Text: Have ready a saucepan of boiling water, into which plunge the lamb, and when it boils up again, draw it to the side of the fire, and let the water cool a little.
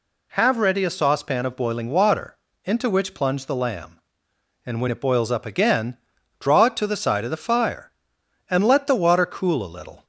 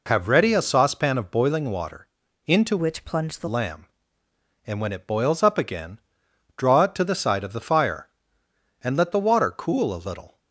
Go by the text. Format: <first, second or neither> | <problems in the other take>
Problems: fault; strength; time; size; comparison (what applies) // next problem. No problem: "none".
first | changes voice from "which" to "the"; from 2.7 to 3.4 s; 0.7 s long